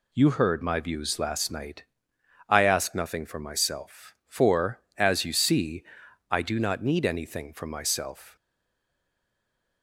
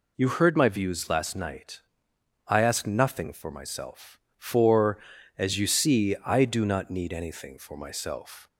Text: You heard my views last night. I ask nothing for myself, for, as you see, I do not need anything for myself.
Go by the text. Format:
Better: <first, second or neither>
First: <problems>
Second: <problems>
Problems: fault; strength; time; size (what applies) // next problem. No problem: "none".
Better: second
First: stays silent after the last word; noticeable; from 8.3 s on; 1.5 s long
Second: none